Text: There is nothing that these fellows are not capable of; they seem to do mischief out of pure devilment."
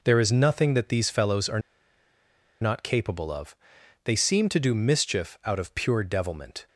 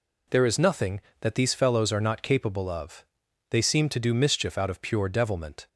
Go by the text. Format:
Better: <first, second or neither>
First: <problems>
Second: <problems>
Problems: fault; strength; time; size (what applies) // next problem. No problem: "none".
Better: second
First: pauses between "are" and "not"; at 1.5 s; 1.0 s long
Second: none